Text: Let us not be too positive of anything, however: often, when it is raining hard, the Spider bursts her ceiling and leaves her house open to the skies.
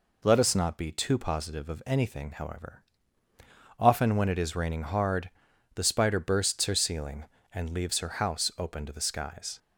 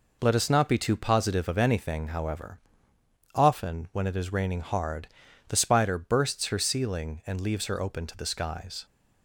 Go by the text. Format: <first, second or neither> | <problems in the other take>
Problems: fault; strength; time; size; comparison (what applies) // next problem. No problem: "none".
first | skips "house"; at 7.8 s